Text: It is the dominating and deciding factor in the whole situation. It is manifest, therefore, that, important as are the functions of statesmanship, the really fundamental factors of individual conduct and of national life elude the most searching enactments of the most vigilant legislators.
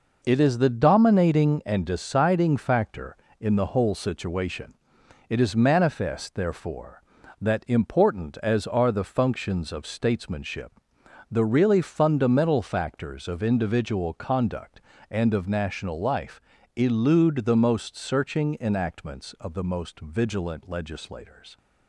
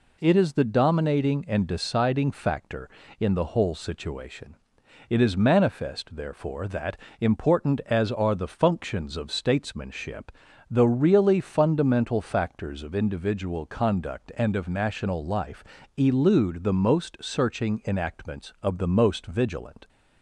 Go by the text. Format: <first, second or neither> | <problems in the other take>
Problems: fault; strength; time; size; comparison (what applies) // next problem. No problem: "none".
first | pauses between "life" and "elude"; slight; at 15.6 s; 0.32 s long; also in the first // stops before "legislators"; at 19.8 s